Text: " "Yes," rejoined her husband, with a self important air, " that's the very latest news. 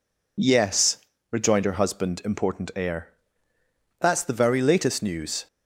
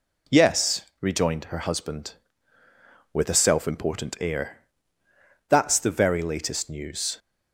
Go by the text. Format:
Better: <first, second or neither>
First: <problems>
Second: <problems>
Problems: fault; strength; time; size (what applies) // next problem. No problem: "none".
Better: second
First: skips "with a self"; at 2.2 s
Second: none